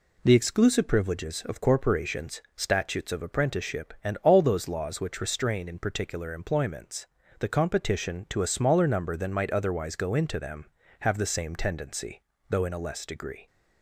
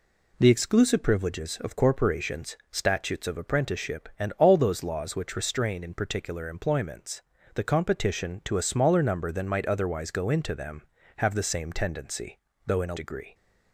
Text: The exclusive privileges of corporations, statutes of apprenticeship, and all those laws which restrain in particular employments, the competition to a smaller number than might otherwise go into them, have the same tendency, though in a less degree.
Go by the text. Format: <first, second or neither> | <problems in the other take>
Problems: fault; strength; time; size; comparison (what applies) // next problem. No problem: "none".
first | skips "less"; at 12.9 s